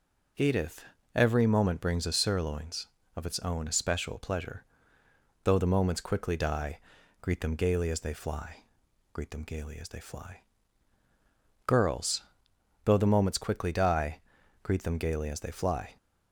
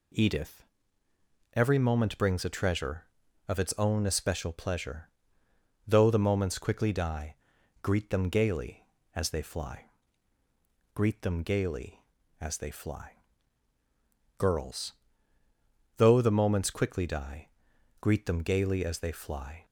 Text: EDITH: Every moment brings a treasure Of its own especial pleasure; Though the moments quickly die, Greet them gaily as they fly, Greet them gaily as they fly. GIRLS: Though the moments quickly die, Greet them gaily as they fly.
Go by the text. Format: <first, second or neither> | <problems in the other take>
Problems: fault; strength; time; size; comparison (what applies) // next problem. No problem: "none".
second | says "sirloins" for "treasure"; at 2.1 s